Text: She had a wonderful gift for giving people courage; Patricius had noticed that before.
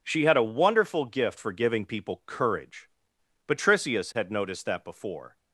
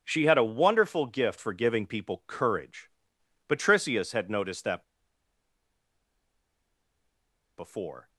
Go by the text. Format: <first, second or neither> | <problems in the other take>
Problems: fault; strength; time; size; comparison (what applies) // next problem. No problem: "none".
first | pauses between "that" and "before"; strong; at 4.8 s; 2.7 s long